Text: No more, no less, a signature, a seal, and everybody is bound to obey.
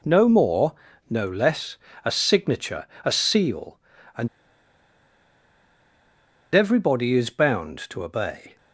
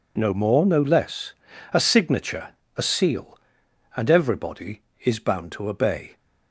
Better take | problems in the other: second | pauses between "and" and "everybody"; strong; at 4.2 s; 2.2 s long

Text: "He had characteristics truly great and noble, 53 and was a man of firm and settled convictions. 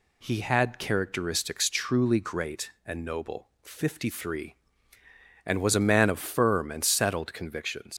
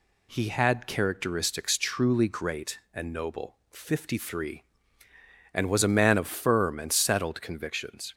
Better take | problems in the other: second | leaves "convictions" unfinished; at 7.9 s; 90 ms

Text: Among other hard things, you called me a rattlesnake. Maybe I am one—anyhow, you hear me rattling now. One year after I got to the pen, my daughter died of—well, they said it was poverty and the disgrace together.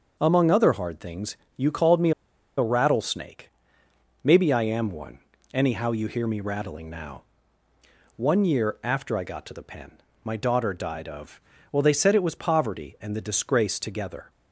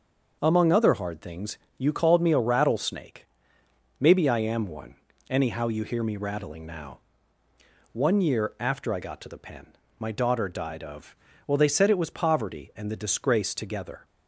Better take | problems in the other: second | starts louder than the rest; noticeable; until 1.2 s; 6 dB; noticeable in the second // pauses between "me" and "a"; noticeable; at 2.1 s; 0.46 s long

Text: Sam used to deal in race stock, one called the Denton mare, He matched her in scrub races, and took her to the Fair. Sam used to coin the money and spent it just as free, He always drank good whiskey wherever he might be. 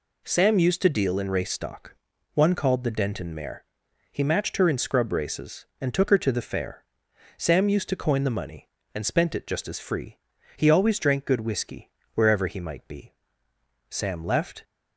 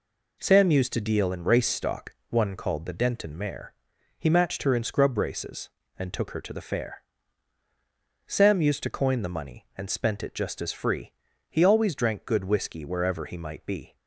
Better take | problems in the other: second | pauses between "whiskey" and "wherever"; slight; at 11.9 s; 0.24 s long // goes on to say "Sam left"; noticeable; from 13.8 s on; 0.74 s long

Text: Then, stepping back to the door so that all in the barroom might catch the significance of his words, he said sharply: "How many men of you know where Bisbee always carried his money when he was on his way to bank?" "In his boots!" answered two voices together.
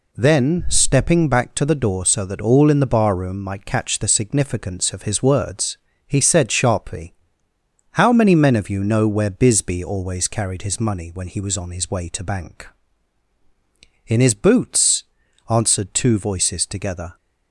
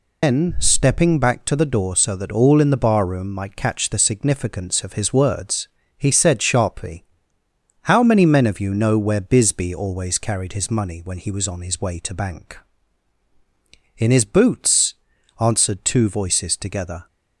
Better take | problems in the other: first | loses the start of "Then"; at 0.2 s; 185 ms

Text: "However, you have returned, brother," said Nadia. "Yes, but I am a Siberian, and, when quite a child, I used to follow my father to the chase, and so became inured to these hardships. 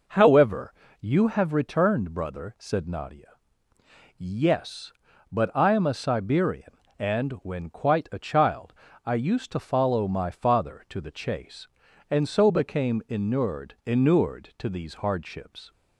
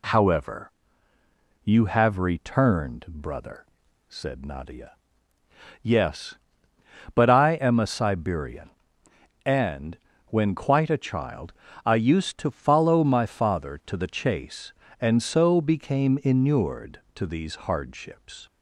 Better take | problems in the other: second | says "inured" twice; at 13.8 s

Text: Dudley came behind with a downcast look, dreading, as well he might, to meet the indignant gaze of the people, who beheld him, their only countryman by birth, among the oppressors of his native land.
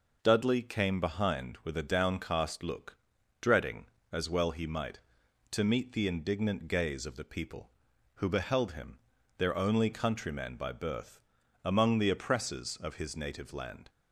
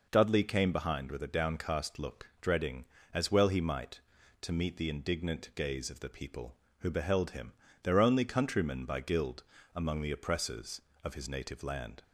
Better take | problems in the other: first | says "guild" for "birth"; at 9.0 s

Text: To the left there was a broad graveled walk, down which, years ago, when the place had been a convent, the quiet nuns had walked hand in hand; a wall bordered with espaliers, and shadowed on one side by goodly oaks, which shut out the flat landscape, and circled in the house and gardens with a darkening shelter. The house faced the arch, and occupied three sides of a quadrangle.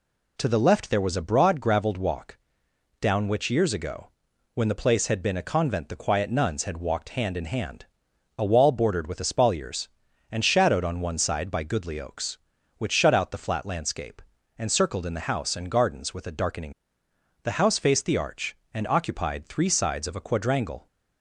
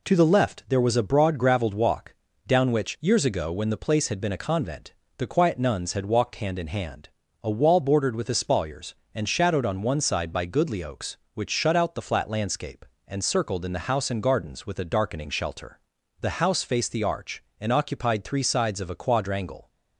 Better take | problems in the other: second | skips "shelter"; at 17.0 s

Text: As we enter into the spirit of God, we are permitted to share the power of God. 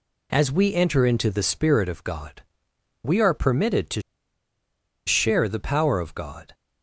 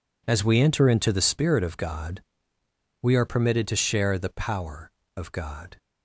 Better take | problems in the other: second | pauses between "to" and "share"; at 4.0 s; 1.0 s long

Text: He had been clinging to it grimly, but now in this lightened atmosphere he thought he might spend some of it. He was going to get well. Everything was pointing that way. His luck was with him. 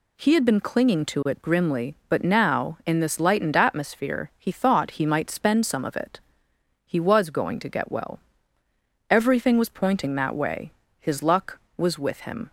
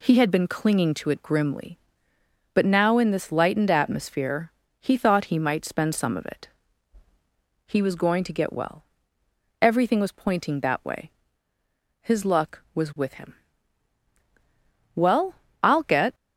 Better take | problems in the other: first | pauses between "atmosphere" and "he"; slight; at 4.5 s; 0.28 s long // goes on to say "Well I'll get"; noticeable; from 14.9 s on; 1.2 s long

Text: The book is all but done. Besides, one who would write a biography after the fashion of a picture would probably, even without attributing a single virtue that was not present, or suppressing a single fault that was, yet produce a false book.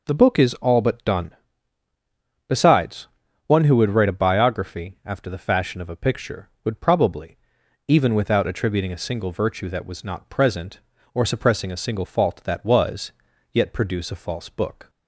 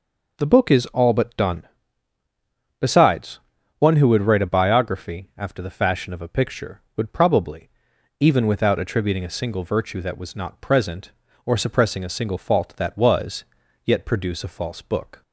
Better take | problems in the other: neither | none

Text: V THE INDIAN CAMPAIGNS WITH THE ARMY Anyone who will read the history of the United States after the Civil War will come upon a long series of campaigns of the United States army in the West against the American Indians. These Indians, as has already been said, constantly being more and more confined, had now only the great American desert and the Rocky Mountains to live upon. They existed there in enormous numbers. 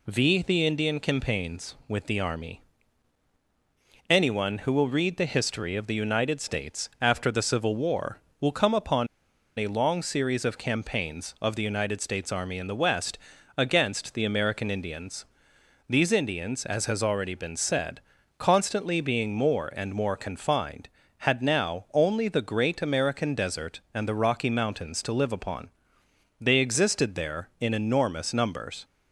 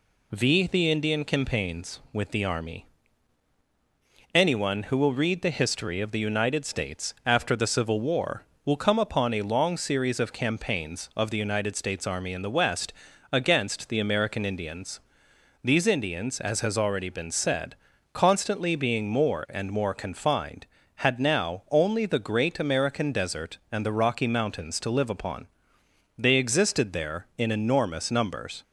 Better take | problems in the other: second | pauses between "ARMY" and "Anyone"; strong; at 2.6 s; 1.5 s long; strong in the second // pauses between "upon" and "a"; noticeable; at 9.0 s; 0.51 s long // pauses between "West" and "against"; at 13.1 s; 0.40 s long; also in the second

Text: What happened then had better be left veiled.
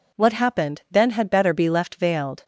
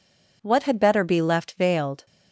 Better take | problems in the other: first | skips "happened then"; at 0.6 s

